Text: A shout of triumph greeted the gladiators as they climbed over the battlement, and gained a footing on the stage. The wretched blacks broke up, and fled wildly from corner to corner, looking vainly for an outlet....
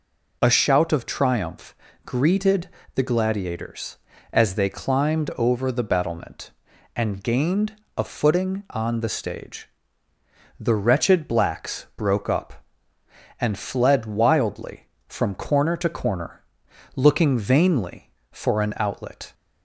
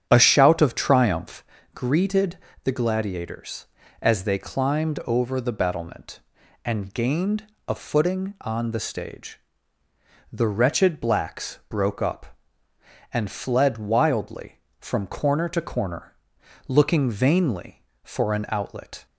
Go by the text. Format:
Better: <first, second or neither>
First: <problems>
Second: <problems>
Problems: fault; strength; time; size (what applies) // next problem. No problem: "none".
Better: first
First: pauses between "triumph" and "greeted"; slight; at 1.7 s; 0.30 s long // pauses between "greeted" and "the"; slight; at 2.6 s; 0.28 s long // pauses between "gained" and "a"; slight; at 7.7 s; 0.20 s long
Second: starts louder than the rest; strong; until 1.6 s; 9 dB // pauses between "triumph" and "greeted"; slight; at 1.4 s; 0.30 s long // pauses between "greeted" and "the"; slight; at 2.3 s; 0.28 s long // pauses between "gained" and "a"; slight; at 7.4 s; 0.20 s long